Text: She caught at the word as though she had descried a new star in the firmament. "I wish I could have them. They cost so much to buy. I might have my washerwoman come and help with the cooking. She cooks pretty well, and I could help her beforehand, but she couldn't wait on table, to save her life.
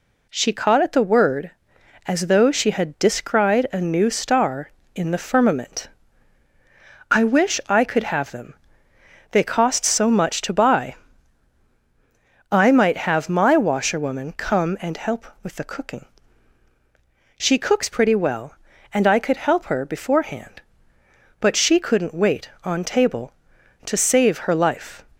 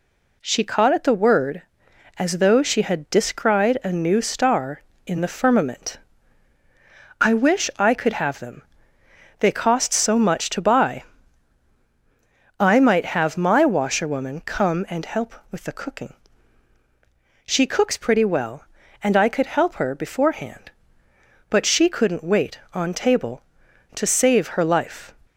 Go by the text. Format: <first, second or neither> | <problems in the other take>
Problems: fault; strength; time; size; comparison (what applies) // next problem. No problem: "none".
neither | none